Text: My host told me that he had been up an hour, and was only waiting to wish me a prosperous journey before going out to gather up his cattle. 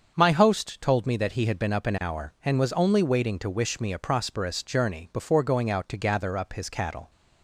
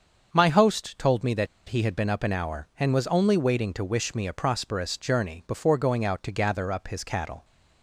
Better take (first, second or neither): first